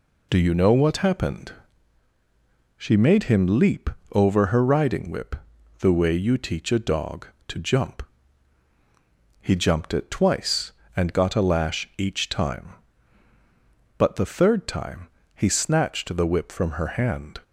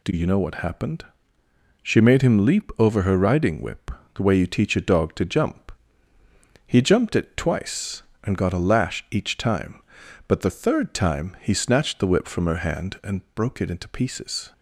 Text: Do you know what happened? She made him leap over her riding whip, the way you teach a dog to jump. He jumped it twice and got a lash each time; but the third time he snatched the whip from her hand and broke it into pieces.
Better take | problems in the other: second | pauses between "leap" and "over"; slight; at 3.8 s; 0.22 s long // pauses between "time" and "he"; slight; at 15.0 s; 0.28 s long // stops before "and broke it into pieces"; at 17.4 s

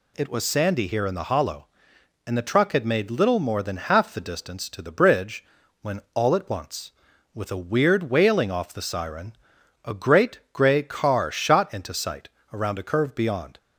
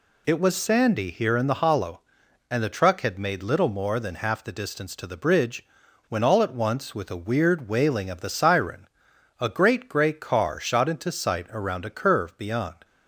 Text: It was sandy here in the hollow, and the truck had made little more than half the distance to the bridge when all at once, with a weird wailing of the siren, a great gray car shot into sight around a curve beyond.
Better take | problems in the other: second | pauses between "bridge" and "when"; at 5.4 s; 0.38 s long; also in the second // says "off" for "of"; at 8.5 s // pauses between "sight" and "around"; slight; at 12.2 s; 0.22 s long

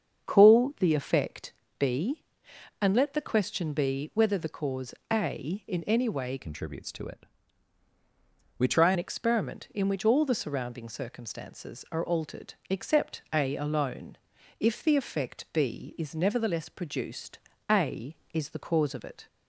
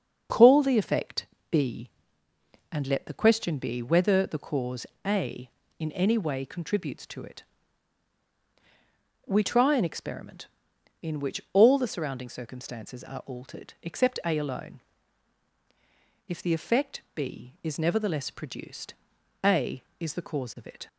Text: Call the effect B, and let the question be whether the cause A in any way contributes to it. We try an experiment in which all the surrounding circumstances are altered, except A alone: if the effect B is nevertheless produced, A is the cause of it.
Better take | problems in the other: second | starts louder than the rest; strong; until 1.3 s; 7 dB; also in the second // pauses between "effect" and "B"; slight; at 1.5 s; 0.26 s long; slight in the second // pauses between "cause" and "A"; slight; at 4.9 s; 0.18 s long; slight in the second // changes voice from "contributes" to "try"; from 6.3 to 8.9 s; 2.6 s long

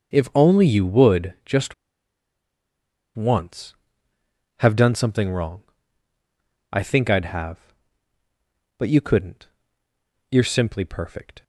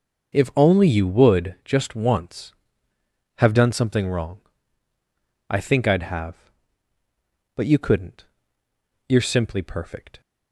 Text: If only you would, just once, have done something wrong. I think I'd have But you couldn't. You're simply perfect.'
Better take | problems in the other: second | pauses between "just" and "once"; strong; at 1.7 s; 1.4 s long

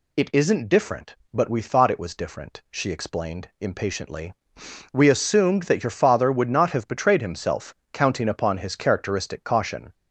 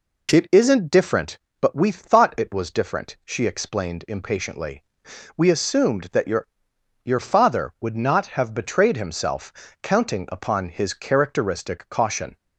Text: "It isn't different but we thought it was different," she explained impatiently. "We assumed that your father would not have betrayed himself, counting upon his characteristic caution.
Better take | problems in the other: first | says "your" twice; at 7.0 s

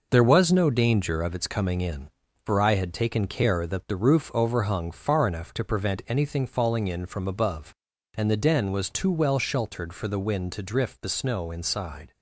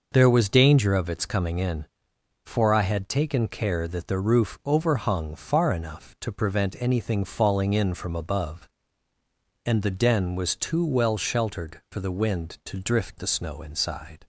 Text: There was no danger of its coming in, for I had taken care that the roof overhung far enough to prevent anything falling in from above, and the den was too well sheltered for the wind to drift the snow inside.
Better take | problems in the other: first | skips "no"; at 0.4 s

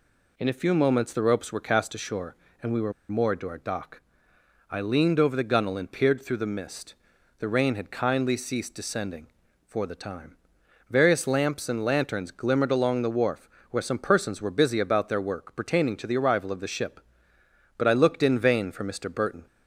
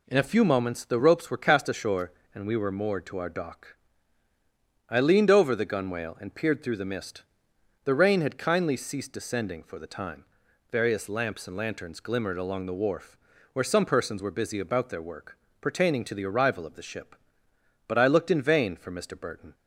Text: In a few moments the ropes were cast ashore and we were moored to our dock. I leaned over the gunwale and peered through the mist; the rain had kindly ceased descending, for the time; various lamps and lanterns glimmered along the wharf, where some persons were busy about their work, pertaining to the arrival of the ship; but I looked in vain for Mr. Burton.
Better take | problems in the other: second | pauses between "were" and "moored"; slight; at 2.9 s; 0.17 s long

